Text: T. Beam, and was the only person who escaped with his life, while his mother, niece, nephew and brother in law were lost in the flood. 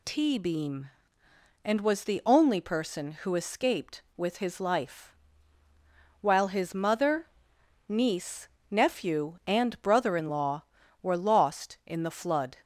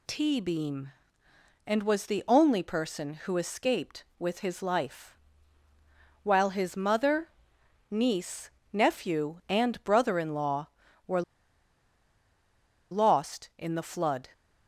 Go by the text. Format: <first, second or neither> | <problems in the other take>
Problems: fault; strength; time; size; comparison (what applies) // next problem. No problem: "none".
first | pauses between "were" and "lost"; strong; at 11.2 s; 1.6 s long